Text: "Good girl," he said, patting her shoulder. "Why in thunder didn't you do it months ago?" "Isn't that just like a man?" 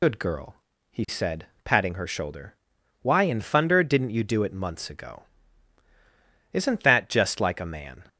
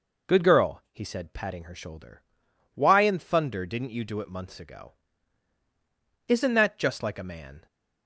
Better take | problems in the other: second | loses the start of "Good"; at 0.0 s; 55 ms

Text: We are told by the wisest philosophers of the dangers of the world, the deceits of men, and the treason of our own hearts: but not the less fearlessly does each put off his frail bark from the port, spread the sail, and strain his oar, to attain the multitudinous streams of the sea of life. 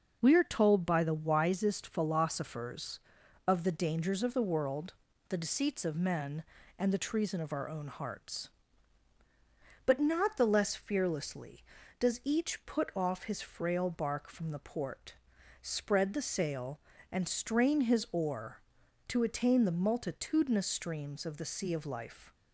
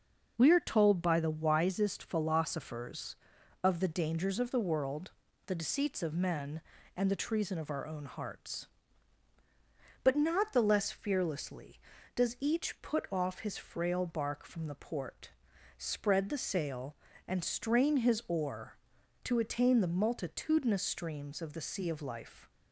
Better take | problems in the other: neither | none

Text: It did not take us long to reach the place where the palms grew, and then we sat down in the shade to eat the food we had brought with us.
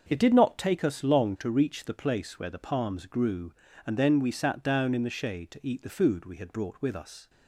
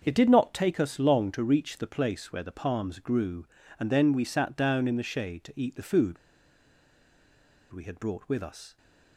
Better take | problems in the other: first | starts louder than the rest; until 1.0 s; 6.5 dB; also in the first // pauses between "food" and "we"; strong; at 6.1 s; 1.5 s long

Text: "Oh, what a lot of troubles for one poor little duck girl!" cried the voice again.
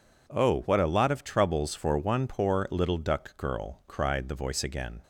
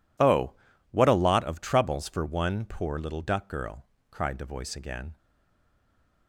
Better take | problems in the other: first | stays silent after the last word; from 5.1 s on; 1.1 s long

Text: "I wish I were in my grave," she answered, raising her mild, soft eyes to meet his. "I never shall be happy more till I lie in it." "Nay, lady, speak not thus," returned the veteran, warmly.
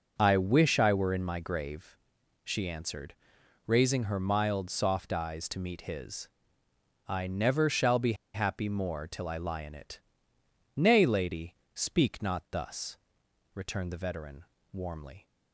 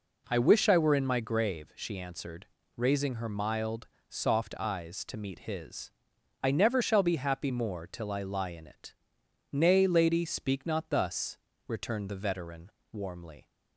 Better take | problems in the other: second | pauses between "be" and "happy"; slight; at 8.1 s; 0.20 s long

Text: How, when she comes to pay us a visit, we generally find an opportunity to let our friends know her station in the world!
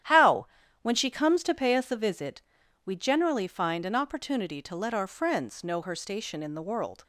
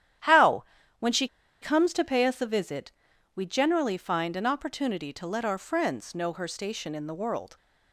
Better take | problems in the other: first | starts louder than the rest; strong; until 1.9 s; 11 dB; strong in the first // pauses between "she" and "comes"; slight; at 1.2 s; 0.32 s long

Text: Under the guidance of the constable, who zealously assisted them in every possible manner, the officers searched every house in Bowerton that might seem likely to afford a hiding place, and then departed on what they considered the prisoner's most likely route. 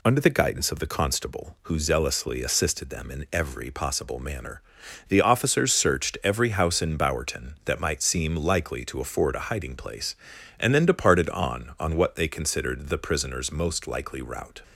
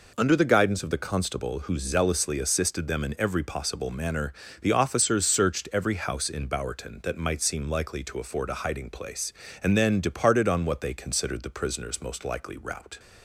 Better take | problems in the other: second | says "on" twice; at 11.7 s

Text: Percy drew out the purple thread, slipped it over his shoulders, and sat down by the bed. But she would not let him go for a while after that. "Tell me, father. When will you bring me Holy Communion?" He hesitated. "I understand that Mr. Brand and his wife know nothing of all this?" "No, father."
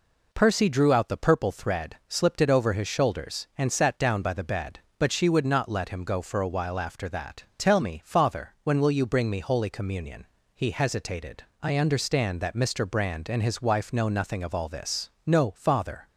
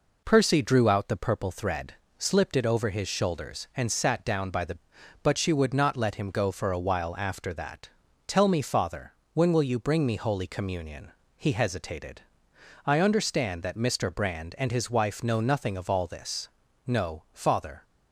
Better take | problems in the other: first | skips "bed"; at 4.9 s

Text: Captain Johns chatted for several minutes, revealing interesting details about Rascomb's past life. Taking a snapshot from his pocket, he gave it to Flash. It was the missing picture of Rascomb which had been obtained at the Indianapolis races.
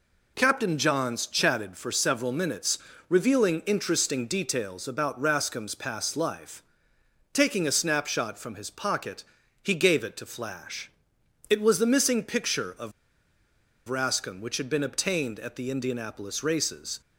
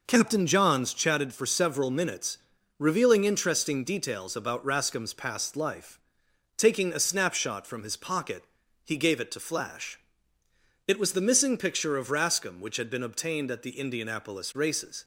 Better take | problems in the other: second | pauses between "of" and "Rascomb"; noticeable; at 12.9 s; 0.96 s long

